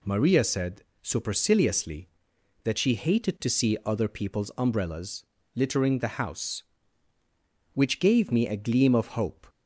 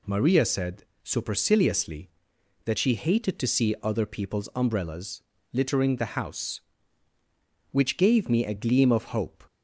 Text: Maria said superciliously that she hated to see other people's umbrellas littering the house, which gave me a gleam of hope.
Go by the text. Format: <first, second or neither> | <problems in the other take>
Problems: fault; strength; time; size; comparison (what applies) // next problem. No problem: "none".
neither | pauses between "said" and "superciliously"; slight; the same in both // pauses between "umbrellas" and "littering"; slight; the same in both